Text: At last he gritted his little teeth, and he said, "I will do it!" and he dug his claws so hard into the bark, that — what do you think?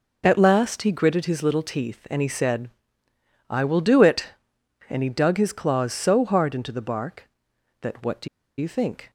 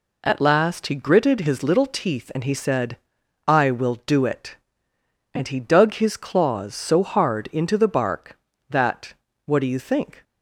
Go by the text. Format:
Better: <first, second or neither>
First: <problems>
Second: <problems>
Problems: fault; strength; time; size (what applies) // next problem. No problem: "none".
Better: second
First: pauses between "do" and "you"; slight; at 8.2 s; 0.32 s long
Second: none